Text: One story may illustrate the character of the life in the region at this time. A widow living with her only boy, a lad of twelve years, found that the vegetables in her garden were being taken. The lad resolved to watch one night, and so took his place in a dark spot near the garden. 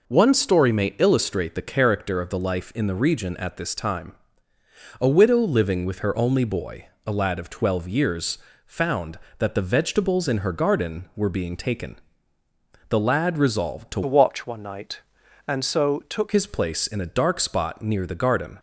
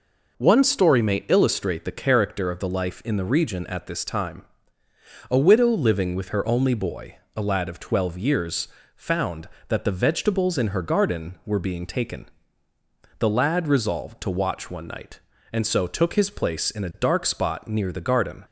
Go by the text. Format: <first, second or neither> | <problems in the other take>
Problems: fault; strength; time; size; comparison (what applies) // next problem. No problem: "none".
second | changes voice from "watch" to "took"; from 14.0 to 16.3 s; 2.3 s long